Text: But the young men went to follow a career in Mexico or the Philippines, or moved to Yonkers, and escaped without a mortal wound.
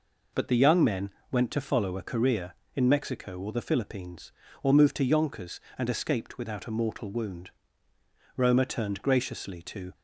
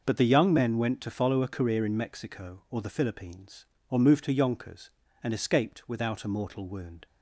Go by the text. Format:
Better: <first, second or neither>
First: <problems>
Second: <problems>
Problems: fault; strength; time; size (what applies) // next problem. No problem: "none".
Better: second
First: pauses between "men" and "went"; slight; at 1.1 s; 0.20 s long // goes on to say "Roma turned graciously to"; from 8.3 s on; 1.5 s long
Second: none